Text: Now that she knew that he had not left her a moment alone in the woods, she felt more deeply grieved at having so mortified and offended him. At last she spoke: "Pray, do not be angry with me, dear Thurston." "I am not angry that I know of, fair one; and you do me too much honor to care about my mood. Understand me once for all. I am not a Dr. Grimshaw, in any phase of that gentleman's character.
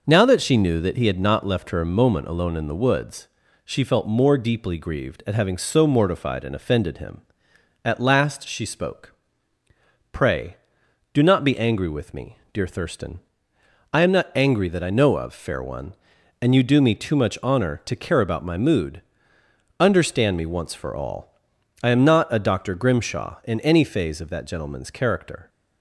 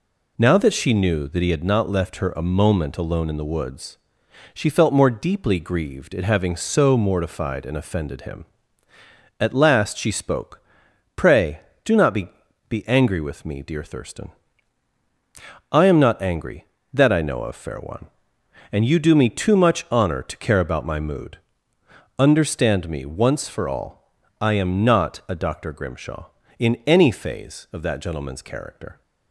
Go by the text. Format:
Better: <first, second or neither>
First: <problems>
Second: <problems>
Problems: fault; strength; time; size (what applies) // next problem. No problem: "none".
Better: first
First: none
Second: says "be" twice; at 12.6 s